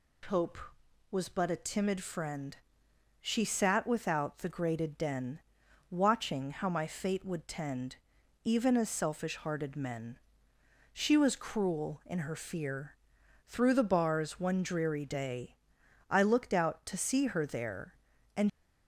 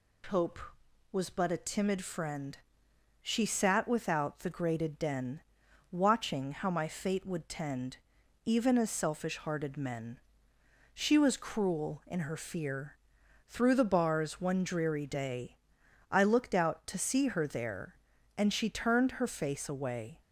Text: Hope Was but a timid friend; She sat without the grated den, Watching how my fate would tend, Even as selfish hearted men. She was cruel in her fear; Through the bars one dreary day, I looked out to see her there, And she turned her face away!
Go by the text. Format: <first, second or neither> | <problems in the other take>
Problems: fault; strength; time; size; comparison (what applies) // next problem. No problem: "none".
second | stops before "she turned her face away"; at 18.4 s